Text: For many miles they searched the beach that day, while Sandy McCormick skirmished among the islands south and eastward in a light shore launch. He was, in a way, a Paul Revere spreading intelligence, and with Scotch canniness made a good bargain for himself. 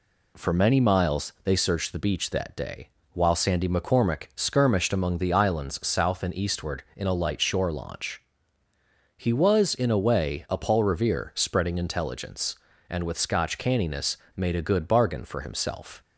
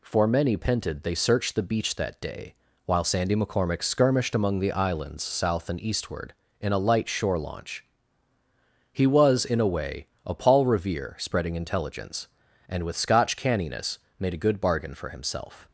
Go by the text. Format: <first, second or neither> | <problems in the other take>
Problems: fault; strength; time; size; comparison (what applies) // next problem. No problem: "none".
first | says "pented" for "miles"; at 0.5 s // pauses between "canniness" and "made"; slight; at 13.9 s; 0.20 s long; slight in the first